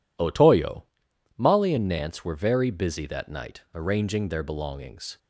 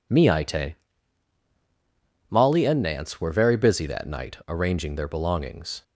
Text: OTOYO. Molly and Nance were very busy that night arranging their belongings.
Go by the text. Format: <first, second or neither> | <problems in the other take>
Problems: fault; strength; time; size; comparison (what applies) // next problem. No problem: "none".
first | says "Miite" for "OTOYO"; at 0.1 s